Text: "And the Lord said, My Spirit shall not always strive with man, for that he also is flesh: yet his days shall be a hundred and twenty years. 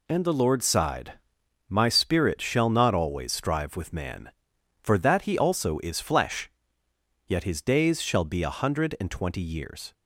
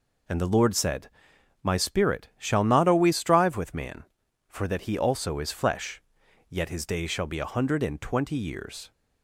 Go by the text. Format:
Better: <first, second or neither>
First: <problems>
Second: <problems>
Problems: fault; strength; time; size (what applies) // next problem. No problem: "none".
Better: second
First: says "sighed" for "said"; at 0.6 s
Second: none